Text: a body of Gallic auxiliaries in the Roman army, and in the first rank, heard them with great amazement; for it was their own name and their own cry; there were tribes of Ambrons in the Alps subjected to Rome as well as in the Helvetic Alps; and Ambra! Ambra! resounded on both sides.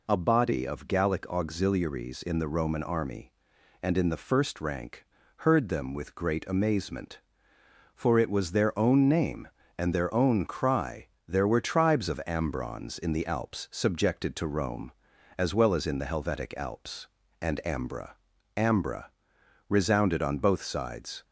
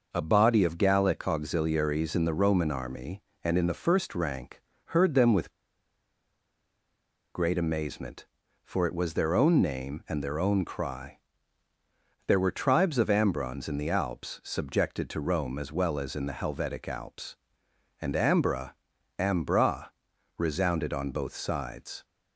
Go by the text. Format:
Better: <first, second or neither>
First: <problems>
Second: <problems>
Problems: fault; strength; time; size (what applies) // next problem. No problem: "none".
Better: first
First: none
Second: pauses between "with" and "great"; strong; at 5.5 s; 1.8 s long